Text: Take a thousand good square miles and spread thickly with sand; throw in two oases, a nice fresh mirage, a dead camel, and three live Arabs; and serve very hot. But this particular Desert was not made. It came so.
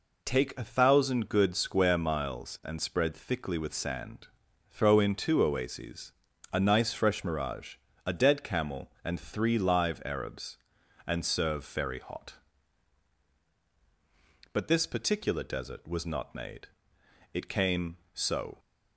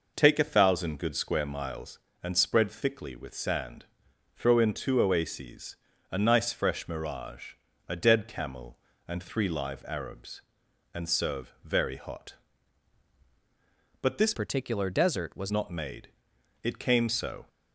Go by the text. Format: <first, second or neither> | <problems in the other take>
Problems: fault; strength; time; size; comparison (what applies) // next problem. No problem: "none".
first | changes voice from "particular" to "was"; from 14.3 to 15.5 s; 1.2 s long